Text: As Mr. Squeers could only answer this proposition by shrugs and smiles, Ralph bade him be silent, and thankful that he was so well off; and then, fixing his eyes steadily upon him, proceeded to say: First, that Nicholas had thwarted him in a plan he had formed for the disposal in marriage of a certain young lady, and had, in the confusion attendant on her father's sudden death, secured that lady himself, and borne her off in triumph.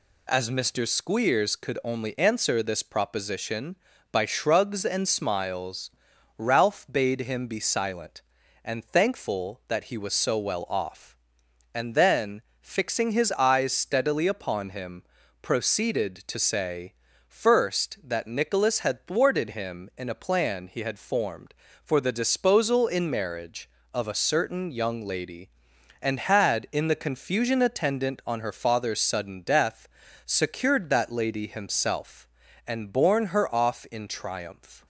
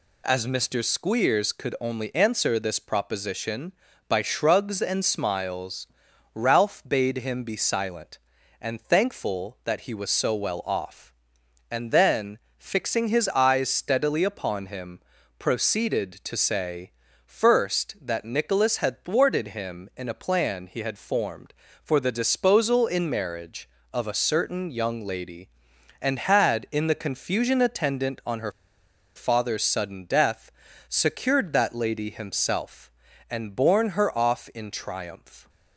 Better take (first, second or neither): first